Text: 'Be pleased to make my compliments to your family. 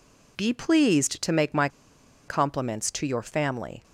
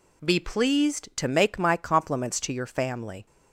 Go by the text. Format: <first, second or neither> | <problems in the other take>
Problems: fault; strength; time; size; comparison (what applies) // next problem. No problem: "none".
second | pauses between "my" and "compliments"; noticeable; at 1.6 s; 0.59 s long